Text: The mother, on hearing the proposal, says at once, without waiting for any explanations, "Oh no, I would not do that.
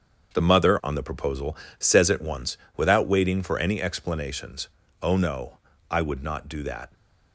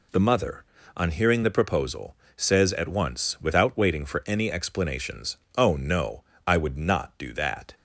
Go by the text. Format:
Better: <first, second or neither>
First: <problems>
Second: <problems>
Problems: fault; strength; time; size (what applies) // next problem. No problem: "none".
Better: second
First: starts louder than the rest; strong; until 1.3 s; 7 dB // skips "hearing"; at 0.9 s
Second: none